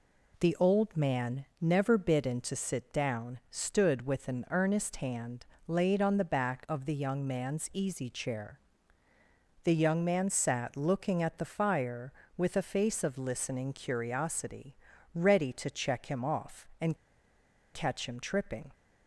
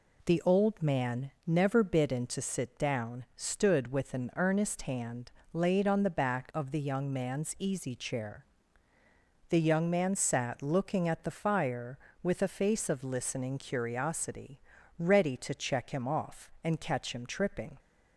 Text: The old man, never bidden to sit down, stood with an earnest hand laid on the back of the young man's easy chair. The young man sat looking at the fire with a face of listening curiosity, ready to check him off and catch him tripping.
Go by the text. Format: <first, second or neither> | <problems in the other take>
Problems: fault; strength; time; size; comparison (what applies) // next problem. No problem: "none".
second | pauses between "hand" and "laid"; slight; at 5.4 s; 0.20 s long; slight in the second // pauses between "and" and "catch"; noticeable; at 16.9 s; 0.77 s long